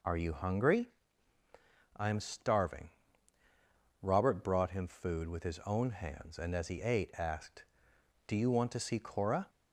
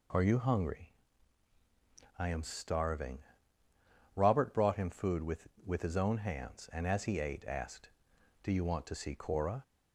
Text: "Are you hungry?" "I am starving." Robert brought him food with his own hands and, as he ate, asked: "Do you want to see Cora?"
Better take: first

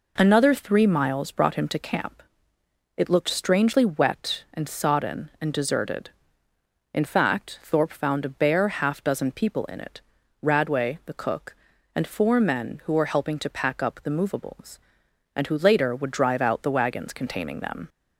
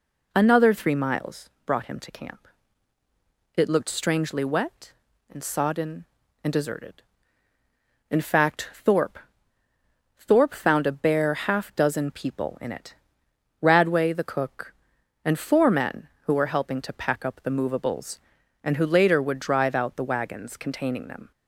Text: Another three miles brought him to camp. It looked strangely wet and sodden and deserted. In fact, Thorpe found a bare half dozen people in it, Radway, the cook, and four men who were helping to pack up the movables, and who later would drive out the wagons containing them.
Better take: first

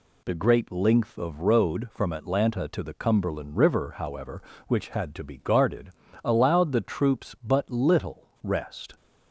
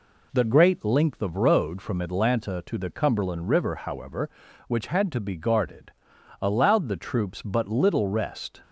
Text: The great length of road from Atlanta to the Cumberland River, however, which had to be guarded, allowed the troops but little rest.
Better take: neither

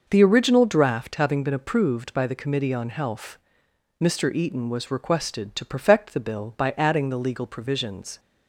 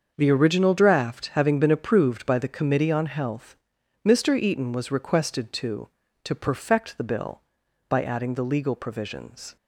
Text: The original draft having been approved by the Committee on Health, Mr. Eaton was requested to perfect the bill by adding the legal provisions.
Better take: first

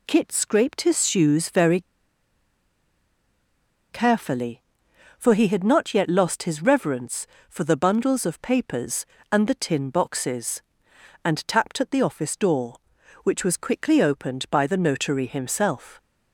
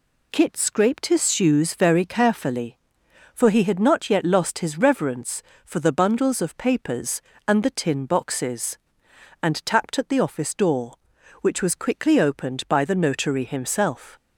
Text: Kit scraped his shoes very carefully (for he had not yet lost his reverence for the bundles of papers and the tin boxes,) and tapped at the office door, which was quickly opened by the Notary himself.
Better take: second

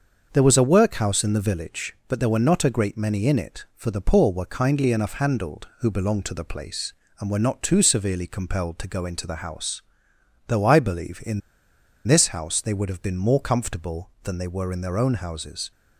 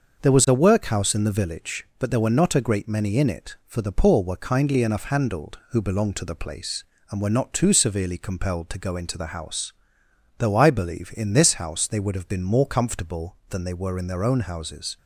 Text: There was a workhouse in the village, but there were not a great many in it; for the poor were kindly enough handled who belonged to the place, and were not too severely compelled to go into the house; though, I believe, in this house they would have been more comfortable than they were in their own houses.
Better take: second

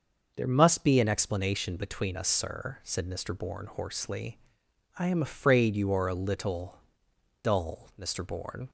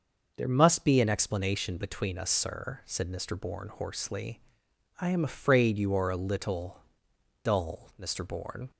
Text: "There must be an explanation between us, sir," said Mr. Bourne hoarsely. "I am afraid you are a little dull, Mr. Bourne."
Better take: neither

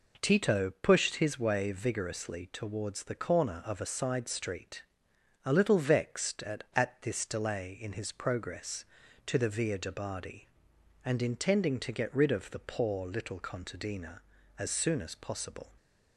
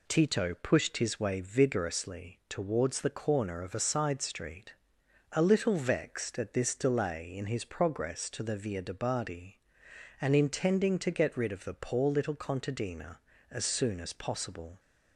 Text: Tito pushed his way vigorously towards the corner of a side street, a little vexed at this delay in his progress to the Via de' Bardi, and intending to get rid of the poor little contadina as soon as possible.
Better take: second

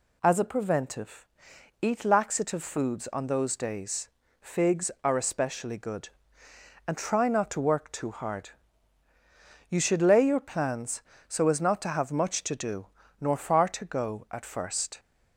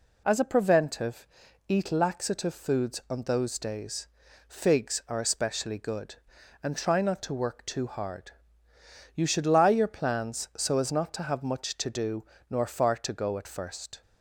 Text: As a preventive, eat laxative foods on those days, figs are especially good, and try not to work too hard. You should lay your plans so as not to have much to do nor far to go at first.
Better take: first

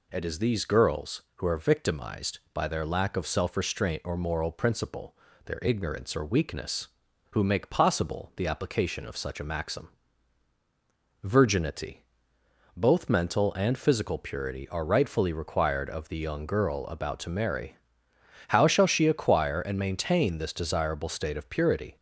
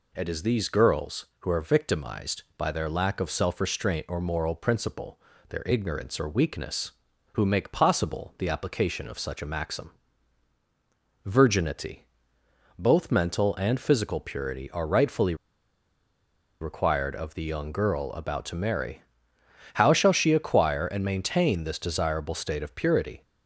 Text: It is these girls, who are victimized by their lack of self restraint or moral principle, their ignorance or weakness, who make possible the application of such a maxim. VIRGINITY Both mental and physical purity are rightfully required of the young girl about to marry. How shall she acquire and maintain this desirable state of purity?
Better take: first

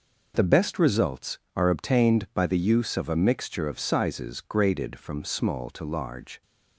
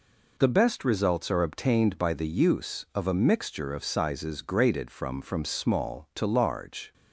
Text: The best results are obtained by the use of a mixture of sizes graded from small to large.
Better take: first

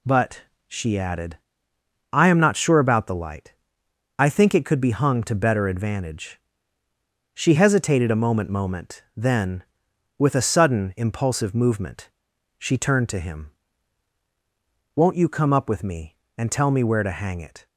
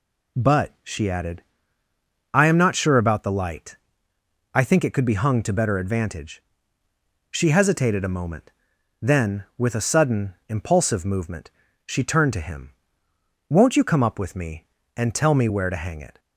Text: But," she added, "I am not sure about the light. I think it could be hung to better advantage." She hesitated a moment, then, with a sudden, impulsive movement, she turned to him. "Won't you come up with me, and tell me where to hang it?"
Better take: second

